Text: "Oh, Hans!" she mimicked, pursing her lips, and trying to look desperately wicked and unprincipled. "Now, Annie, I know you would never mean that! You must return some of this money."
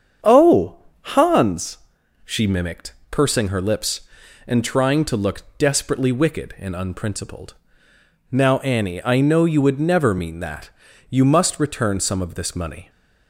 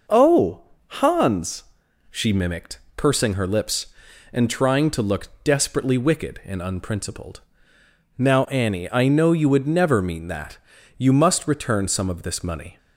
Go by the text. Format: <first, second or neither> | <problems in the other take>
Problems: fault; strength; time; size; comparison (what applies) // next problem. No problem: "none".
second | starts louder than the rest; strong; until 1.5 s; 7.5 dB // pauses between "look" and "desperately"; slight; at 5.4 s; 0.16 s long; slight in the second